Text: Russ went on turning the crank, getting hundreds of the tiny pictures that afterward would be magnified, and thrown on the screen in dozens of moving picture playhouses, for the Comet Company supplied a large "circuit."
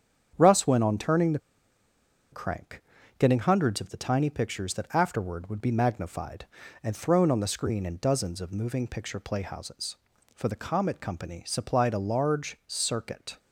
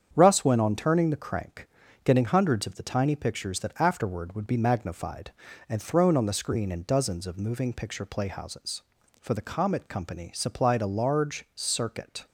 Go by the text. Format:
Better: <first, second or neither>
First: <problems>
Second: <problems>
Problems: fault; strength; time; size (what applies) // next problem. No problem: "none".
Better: second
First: starts louder than the rest; strong; until 1.3 s; 8 dB // pauses between "the" and "crank"; noticeable; at 1.3 s; 0.93 s long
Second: starts louder than the rest; strong; until 1.1 s; 8 dB